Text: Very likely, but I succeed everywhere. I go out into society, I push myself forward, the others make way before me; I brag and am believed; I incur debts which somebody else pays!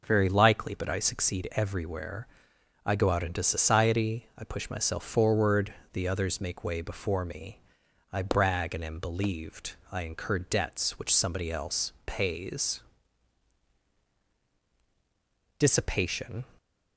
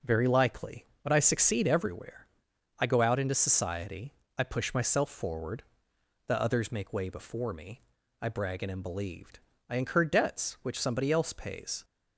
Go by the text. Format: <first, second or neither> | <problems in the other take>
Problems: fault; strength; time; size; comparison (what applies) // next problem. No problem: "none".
second | goes on to say "Dissipation"; noticeable; from 15.5 s on; 0.86 s long